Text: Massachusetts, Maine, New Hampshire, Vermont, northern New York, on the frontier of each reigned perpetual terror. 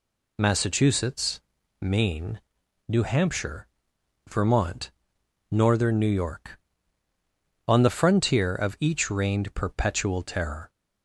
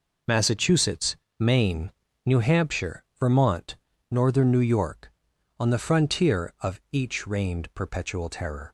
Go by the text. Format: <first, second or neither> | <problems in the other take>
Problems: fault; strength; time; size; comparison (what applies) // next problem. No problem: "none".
neither | none